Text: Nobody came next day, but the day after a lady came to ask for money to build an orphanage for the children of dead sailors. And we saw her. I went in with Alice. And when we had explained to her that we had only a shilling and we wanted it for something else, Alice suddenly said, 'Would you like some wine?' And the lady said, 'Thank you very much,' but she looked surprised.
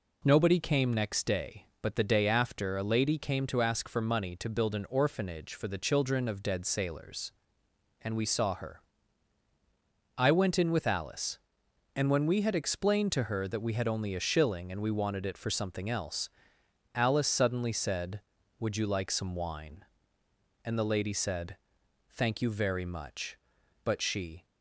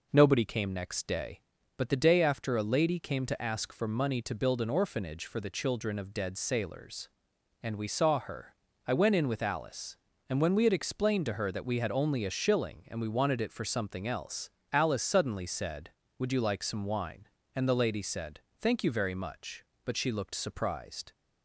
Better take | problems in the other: second | stops before "looked surprised"; at 24.4 s

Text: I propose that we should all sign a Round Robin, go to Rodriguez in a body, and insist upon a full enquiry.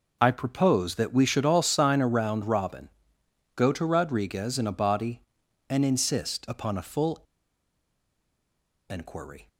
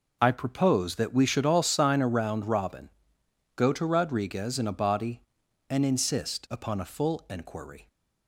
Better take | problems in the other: second | pauses between "full" and "enquiry"; strong; at 7.2 s; 1.6 s long

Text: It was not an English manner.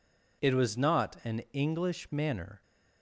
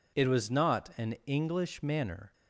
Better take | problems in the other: neither | none

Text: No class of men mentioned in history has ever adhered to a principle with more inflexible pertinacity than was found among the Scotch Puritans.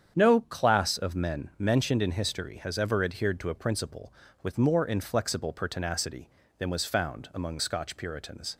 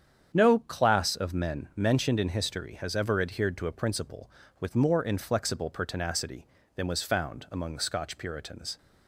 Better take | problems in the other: second | starts louder than the rest; strong; until 1.1 s; 8.5 dB; strong in the second // skips "the"; at 7.5 s

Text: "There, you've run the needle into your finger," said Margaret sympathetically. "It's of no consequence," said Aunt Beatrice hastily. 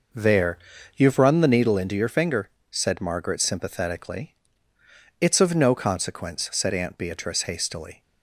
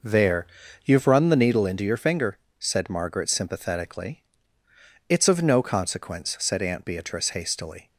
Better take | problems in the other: neither | none

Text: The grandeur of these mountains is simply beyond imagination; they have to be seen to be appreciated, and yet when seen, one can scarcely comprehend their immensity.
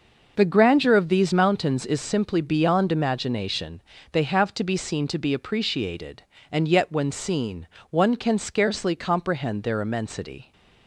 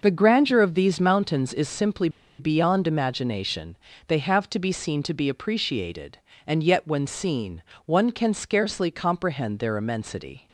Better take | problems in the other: first | pauses between "simply" and "beyond"; slight; at 2.0 s; 0.30 s long

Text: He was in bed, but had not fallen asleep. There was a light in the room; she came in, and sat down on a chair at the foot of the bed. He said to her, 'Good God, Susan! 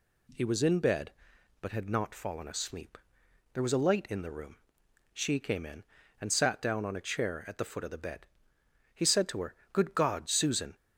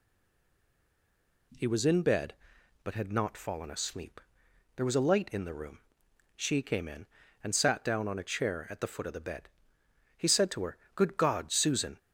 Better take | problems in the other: first | stays silent before the first word; noticeable; until 1.5 s; 1.5 s long

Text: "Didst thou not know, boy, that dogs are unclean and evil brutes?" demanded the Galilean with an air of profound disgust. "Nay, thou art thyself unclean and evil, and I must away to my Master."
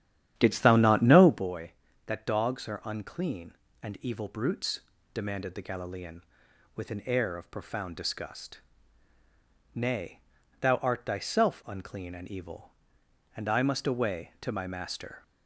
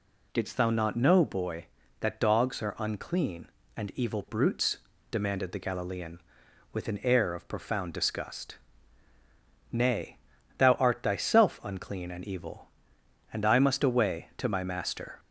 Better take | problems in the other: second | starts louder than the rest; strong; until 1.5 s; 10 dB

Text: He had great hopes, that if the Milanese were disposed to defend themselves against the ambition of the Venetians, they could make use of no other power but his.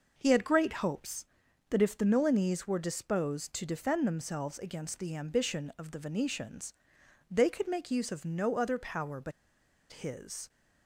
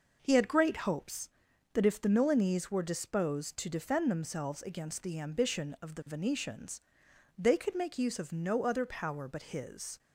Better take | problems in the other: second | pauses between "but" and "his"; noticeable; at 9.3 s; 0.60 s long

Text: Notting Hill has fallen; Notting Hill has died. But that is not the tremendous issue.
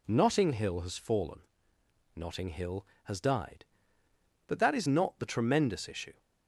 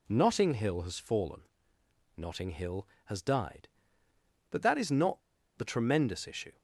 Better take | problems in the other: first | pauses between "not" and "the"; at 5.2 s; 0.37 s long

